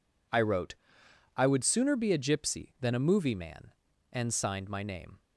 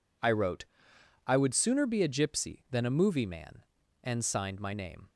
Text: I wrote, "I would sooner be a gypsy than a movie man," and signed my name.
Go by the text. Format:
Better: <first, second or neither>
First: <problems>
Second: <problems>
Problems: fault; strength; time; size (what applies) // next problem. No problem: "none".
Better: neither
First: none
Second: none